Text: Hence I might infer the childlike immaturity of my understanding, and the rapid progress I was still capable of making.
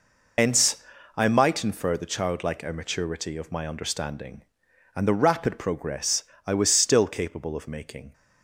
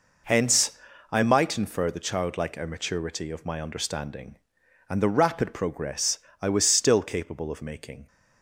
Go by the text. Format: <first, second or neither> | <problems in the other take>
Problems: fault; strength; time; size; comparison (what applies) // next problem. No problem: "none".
second | loses the start of "Hence"; at 0.3 s; 80 ms // pauses between "Hence" and "I"; slight; at 0.8 s; 0.32 s long; slight in the second // pauses between "progress" and "I"; slight; at 6.2 s; 0.22 s long; slight in the second